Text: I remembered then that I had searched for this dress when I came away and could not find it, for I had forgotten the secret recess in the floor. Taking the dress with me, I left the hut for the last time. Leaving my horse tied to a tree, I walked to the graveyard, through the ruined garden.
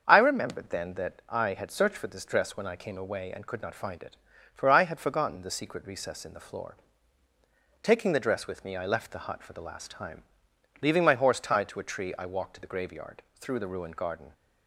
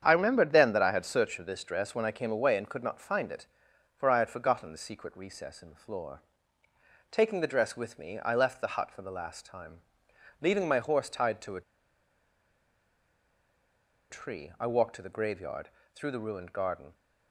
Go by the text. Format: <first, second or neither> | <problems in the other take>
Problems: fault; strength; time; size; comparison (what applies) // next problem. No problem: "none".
first | starts louder than the rest; strong; until 1.0 s; 8 dB; strong in the first // pauses between "a" and "tree"; strong; at 11.6 s; 2.4 s long